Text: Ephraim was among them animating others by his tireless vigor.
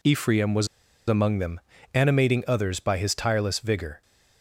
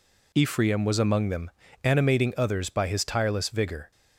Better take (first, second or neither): second